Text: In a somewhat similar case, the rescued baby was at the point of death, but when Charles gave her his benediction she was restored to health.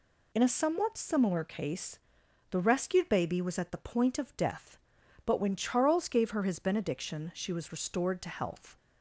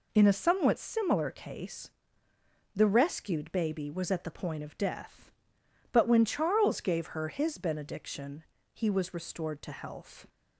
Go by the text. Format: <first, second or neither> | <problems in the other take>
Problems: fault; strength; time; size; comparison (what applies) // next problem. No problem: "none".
first | says "he" for "she"; at 8.7 s